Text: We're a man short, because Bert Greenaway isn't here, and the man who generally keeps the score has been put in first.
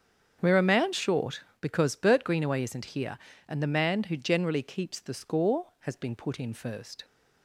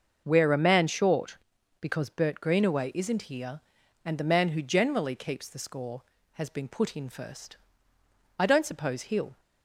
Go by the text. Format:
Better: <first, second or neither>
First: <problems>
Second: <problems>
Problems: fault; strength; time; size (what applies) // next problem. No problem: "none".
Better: first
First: starts louder than the rest; strong; until 1.4 s; 7.5 dB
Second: starts louder than the rest; until 1.2 s; 6.5 dB // goes on to say "I don't suppose he'll"; noticeable; from 8.3 s on; 1.0 s long